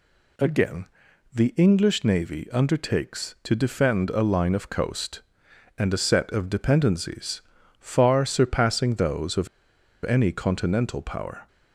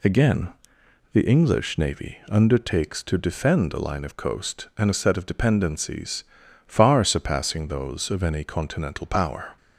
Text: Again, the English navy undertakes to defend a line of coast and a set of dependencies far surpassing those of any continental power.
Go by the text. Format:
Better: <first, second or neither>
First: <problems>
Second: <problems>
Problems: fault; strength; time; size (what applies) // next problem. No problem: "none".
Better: second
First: pauses between "dependencies" and "far"; at 7.4 s; 0.38 s long // pauses between "of" and "any"; noticeable; at 9.4 s; 0.57 s long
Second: pauses between "dependencies" and "far"; noticeable; at 6.2 s; 0.46 s long